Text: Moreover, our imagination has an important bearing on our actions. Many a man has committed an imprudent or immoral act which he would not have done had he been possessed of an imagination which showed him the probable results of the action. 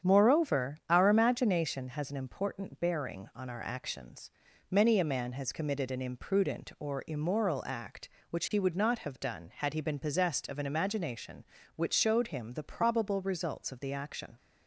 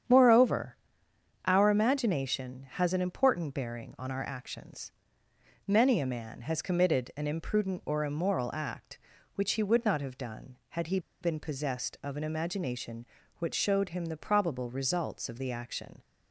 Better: first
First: starts louder than the rest; strong; until 1.1 s; 8 dB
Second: starts louder than the rest; strong; until 1.7 s; 8.5 dB // pauses between "he" and "been"; slight; at 10.9 s; 0.22 s long

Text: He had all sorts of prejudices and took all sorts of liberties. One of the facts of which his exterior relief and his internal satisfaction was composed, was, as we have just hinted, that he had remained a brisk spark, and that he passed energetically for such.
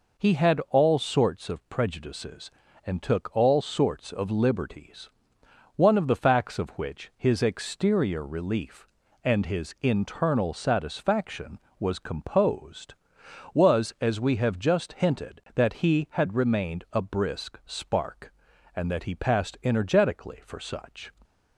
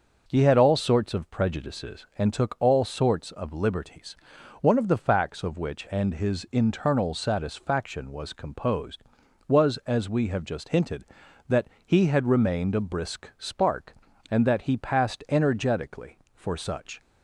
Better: first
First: none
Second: starts louder than the rest; until 1.2 s; 6.5 dB // skips "his exterior relief"; at 5.8 s // pauses between "that" and "he"; slight; at 11.6 s; 0.18 s long

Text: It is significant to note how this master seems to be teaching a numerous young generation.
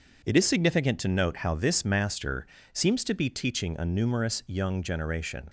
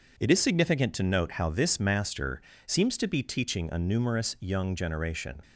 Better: neither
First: pauses between "master" and "seems"; slight; at 2.4 s; 0.28 s long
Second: pauses between "master" and "seems"; slight; at 2.4 s; 0.26 s long

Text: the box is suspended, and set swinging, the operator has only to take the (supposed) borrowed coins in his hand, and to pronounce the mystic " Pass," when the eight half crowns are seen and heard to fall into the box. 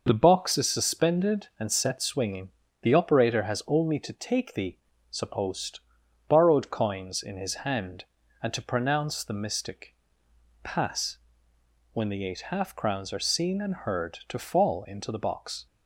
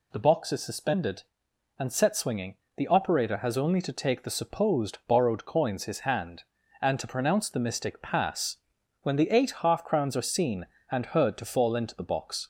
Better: first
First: none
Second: skips "in"; at 5.8 s

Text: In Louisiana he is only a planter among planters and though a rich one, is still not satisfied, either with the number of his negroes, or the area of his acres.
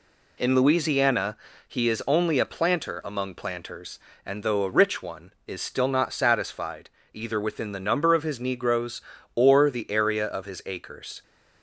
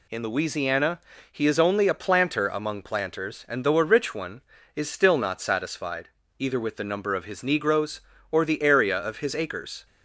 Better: second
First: pauses between "Louisiana" and "he"; slight; at 1.3 s; 0.30 s long // says "within" for "with"; at 7.3 s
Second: pauses between "Louisiana" and "he"; slight; at 0.9 s; 0.32 s long

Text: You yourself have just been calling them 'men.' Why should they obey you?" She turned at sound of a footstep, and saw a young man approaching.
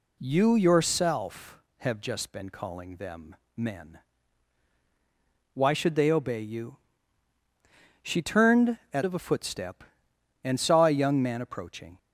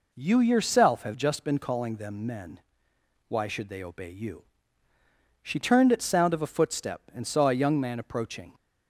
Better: second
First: pauses between "them" and "men"; slight; at 3.3 s; 0.18 s long // skips "sound"; at 9.0 s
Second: none

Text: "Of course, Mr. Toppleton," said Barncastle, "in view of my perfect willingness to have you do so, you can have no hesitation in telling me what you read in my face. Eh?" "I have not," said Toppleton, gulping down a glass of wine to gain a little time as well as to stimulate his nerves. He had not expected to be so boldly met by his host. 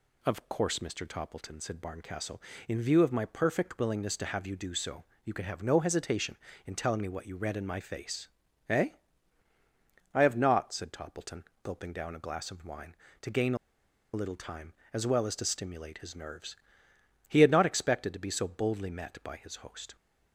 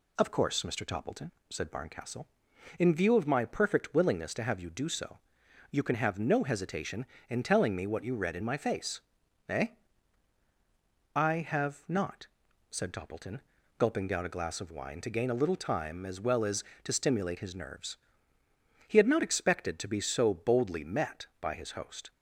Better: second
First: pauses between "a" and "little"; noticeable; at 13.5 s; 0.58 s long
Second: none

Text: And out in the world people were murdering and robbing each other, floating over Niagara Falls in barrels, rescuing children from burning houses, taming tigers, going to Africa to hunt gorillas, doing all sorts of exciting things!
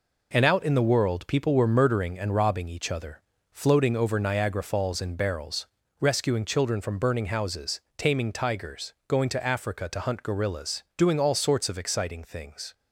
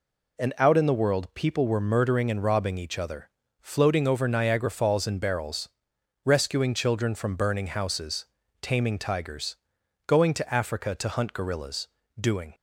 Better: first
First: none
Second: stops before "all sorts of exciting things"; at 12.5 s

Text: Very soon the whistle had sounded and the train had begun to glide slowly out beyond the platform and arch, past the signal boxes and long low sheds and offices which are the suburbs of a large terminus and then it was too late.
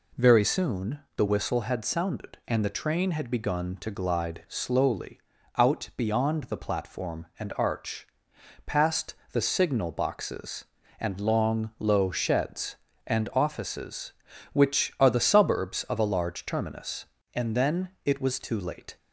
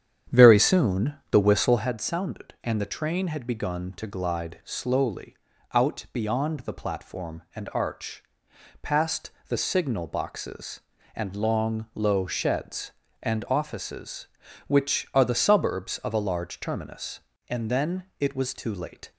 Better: first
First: pauses between "soon" and "the"; slight; at 0.9 s; 0.16 s long // pauses between "slowly" and "out"; slight; at 5.2 s; 0.36 s long // pauses between "past" and "the"; slight; at 9.1 s; 0.18 s long // pauses between "then" and "it"; slight; at 17.8 s; 0.16 s long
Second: starts louder than the rest; strong; until 1.9 s; 9 dB // pauses between "soon" and "the"; slight; at 1.1 s; 0.16 s long // pauses between "slowly" and "out"; slight; at 5.3 s; 0.36 s long // pauses between "past" and "the"; slight; at 9.3 s; 0.18 s long // pauses between "then" and "it"; slight; at 18.0 s; 0.16 s long

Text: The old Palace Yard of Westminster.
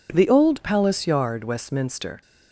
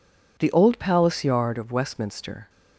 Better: second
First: skips "of"; at 1.4 s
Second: none

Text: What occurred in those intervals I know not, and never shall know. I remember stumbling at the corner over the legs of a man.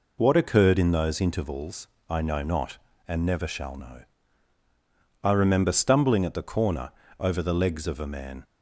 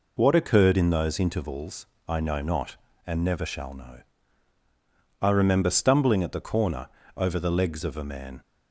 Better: neither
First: pauses between "intervals" and "I"; slight; at 1.8 s; 0.22 s long // pauses between "corner" and "over"; slight; at 6.9 s; 0.30 s long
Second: pauses between "intervals" and "I"; slight; at 1.8 s; 0.22 s long // pauses between "corner" and "over"; slight; at 6.8 s; 0.30 s long

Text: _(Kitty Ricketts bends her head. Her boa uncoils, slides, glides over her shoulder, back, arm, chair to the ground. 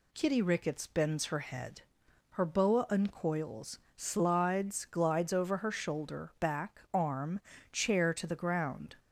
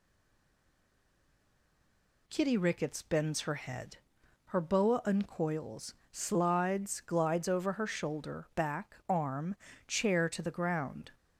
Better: first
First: none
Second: stays silent before the first word; until 2.2 s; 2.2 s long

